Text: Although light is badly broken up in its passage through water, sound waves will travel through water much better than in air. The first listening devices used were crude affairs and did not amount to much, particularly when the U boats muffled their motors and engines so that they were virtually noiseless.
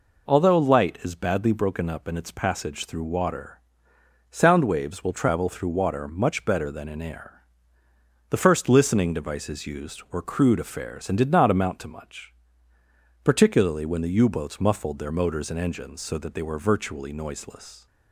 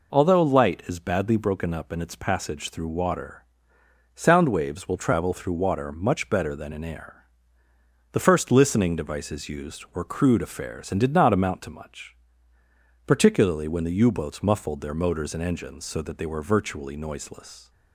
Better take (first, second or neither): neither